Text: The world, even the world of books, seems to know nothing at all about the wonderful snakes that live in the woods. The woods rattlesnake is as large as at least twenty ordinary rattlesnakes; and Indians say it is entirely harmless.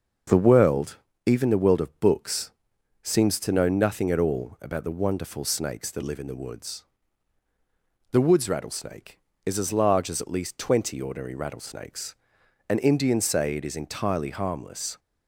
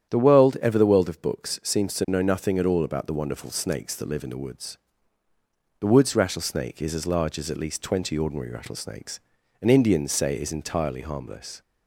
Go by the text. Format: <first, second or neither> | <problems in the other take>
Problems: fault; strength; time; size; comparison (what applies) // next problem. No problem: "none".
first | starts louder than the rest; strong; until 1.1 s; 9.5 dB; also in the first // says "ever" for "even"; at 0.6 s